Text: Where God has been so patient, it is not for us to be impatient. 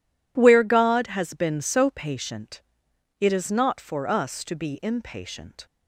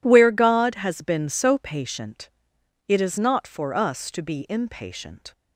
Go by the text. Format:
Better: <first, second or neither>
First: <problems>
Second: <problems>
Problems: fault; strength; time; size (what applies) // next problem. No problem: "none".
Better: neither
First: none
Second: none